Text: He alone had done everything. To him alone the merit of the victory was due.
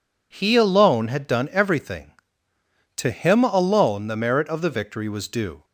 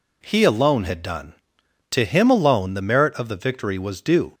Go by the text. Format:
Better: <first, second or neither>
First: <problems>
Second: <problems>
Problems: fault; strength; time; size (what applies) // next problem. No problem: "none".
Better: first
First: none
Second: skips "everything"; at 1.6 s